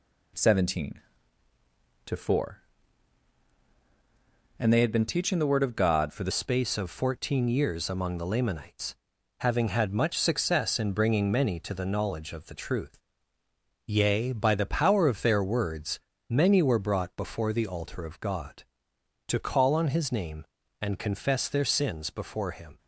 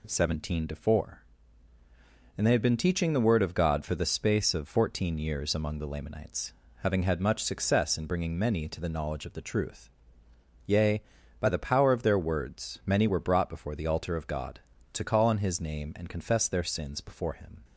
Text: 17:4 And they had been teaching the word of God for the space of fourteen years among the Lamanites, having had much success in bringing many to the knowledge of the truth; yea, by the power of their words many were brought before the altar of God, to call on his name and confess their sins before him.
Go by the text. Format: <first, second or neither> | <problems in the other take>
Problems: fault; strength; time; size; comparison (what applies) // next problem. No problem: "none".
second | changes voice at "space"; from 6.3 s on; 16.4 s long // pauses between "words" and "many"; slight; at 15.9 s; 0.32 s long